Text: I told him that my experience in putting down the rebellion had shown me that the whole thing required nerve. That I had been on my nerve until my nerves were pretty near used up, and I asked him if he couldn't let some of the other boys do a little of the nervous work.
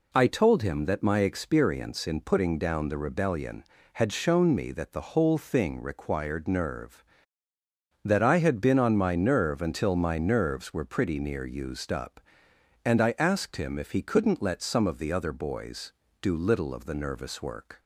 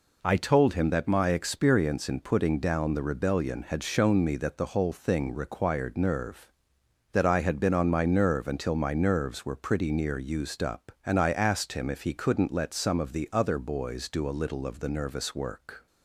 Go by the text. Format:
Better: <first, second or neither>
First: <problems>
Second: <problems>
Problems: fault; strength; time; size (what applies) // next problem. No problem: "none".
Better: second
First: skips "a"; at 16.3 s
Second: none